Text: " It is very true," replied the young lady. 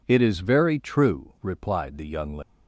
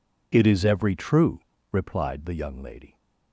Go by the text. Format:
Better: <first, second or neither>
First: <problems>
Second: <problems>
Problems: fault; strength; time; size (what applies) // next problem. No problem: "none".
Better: first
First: none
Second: says "every" for "very"; at 0.6 s